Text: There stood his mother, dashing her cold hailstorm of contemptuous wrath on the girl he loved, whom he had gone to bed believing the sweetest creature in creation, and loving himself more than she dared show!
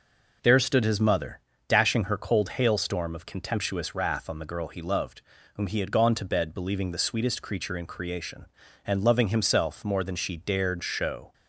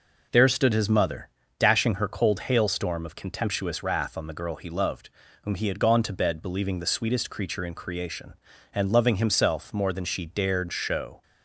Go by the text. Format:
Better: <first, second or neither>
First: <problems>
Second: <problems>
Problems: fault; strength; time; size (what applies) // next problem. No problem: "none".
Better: neither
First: none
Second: none